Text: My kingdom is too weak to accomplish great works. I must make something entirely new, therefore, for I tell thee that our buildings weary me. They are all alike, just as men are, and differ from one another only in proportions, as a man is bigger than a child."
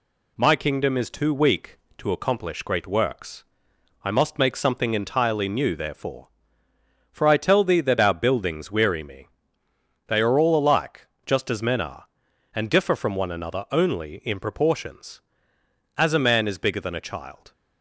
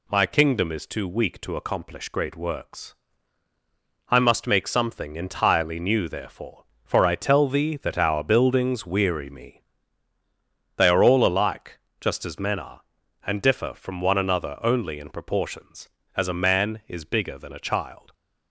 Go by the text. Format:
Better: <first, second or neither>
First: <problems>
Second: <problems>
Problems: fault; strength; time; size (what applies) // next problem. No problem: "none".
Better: neither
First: none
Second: none